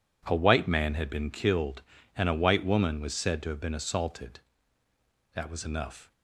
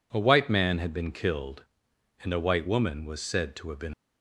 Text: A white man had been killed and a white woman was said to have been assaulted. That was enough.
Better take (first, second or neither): first